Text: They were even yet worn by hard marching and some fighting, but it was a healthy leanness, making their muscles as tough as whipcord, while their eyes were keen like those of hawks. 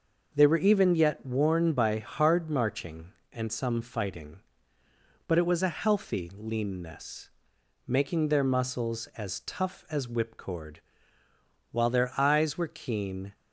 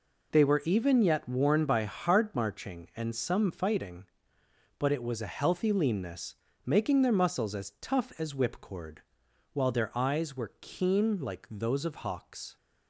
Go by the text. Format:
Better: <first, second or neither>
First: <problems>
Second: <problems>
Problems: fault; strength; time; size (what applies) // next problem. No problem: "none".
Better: second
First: stops before "like those of hawks"; at 13.3 s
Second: none